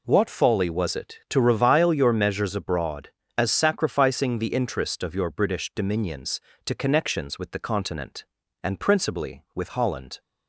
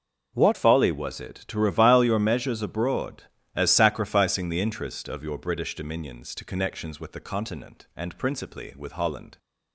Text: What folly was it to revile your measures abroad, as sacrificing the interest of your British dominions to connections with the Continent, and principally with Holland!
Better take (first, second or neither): first